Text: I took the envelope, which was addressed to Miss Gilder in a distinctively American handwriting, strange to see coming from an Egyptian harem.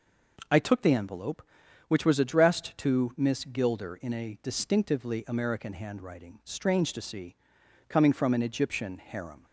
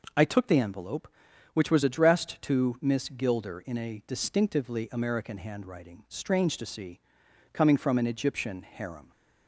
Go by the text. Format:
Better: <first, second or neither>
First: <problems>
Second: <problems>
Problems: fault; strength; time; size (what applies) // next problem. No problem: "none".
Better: neither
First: pauses between "see" and "coming"; noticeable; at 7.3 s; 0.52 s long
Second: pauses between "see" and "coming"; noticeable; at 7.0 s; 0.52 s long